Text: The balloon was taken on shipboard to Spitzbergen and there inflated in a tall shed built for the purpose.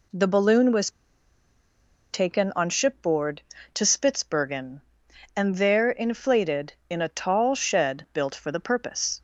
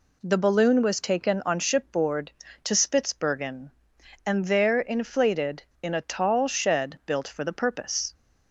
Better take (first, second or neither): second